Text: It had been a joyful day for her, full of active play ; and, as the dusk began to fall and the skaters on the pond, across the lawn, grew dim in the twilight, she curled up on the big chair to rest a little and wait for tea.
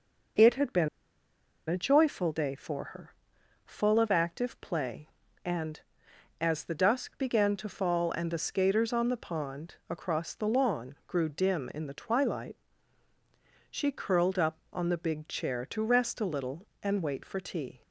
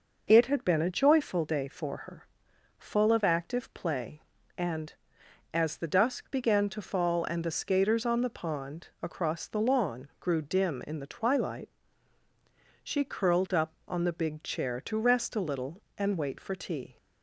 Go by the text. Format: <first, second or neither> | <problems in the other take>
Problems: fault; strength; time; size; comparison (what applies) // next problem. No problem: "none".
second | pauses between "been" and "a"; noticeable; at 0.8 s; 0.81 s long